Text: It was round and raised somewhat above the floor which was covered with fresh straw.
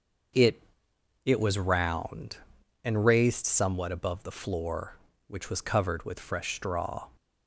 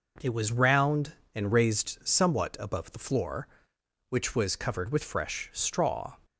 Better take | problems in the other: second | starts louder than the rest; noticeable; until 1.9 s; 6 dB // says "It" twice; at 1.2 s

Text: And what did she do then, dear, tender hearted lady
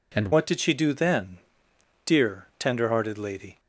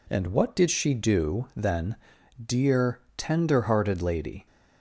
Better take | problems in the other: second | changes voice at "what"; from 0.3 s on; 3.2 s long

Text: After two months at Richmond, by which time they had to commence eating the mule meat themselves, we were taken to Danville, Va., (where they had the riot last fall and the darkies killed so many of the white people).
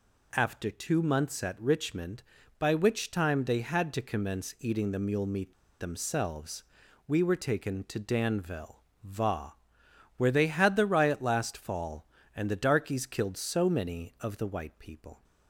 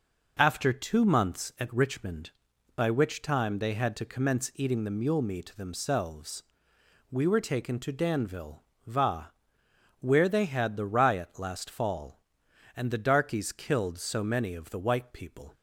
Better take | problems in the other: second | pauses between "meat" and "themselves"; slight; at 5.5 s; 0.25 s long

